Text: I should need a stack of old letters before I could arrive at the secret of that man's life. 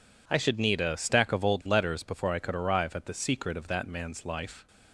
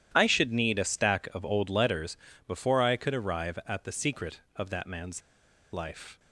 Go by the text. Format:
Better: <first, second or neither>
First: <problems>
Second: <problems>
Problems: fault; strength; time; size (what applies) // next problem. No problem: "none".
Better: first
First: none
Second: pauses between "letters" and "before"; slight; at 2.1 s; 0.28 s long // pauses between "man's" and "life"; noticeable; at 5.2 s; 0.51 s long